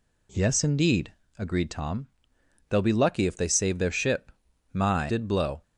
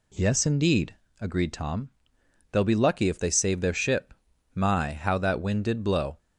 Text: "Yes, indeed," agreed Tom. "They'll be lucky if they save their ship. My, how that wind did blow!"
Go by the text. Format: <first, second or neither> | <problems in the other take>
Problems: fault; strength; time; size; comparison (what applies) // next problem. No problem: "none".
second | skips "how that wind"; at 5.0 s